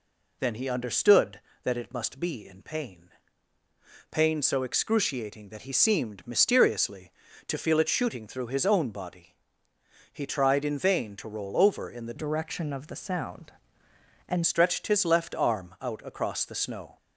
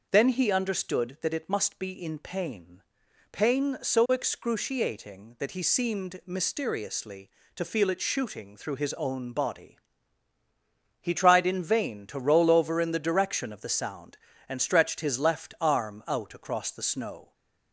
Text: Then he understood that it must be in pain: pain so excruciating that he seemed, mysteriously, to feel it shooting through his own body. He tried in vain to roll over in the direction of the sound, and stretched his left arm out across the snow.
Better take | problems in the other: second | changes voice from "direction" to "and"; from 12.1 to 14.4 s; 2.3 s long

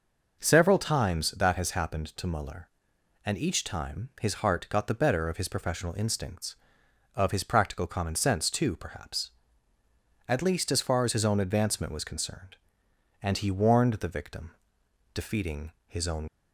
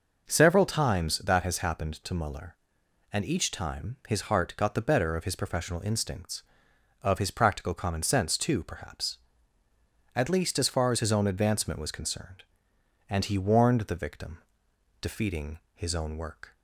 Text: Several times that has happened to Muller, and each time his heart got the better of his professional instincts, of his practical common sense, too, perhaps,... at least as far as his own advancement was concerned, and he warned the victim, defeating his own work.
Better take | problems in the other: second | stops before "work"; at 16.2 s

